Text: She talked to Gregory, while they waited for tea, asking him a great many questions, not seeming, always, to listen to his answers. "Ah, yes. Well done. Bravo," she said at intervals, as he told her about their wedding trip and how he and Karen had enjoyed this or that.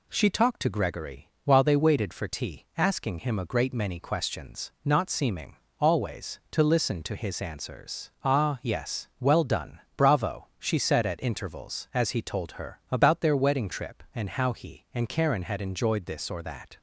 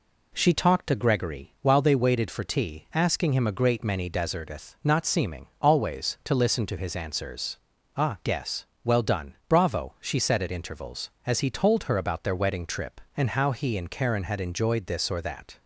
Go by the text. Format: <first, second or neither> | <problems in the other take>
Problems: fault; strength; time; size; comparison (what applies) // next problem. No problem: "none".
first | says "deserteth" for "questions"; at 4.0 s